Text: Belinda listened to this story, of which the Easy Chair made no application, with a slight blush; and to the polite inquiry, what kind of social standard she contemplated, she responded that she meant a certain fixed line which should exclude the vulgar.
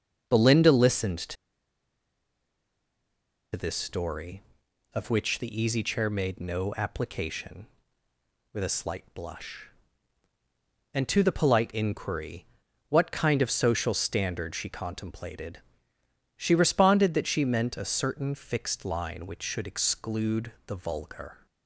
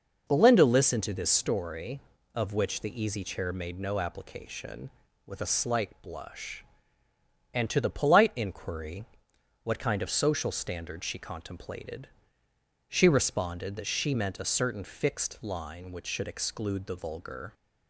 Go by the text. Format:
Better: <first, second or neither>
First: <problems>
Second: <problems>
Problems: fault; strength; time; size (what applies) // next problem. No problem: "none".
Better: second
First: starts louder than the rest; noticeable; until 1.2 s; 6 dB // pauses between "to" and "this"; strong; at 1.3 s; 2.1 s long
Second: none